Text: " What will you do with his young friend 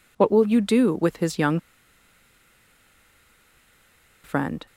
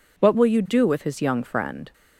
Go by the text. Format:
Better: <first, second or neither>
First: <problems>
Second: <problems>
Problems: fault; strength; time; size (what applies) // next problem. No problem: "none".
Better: second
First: pauses between "young" and "friend"; strong; at 1.5 s; 2.6 s long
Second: none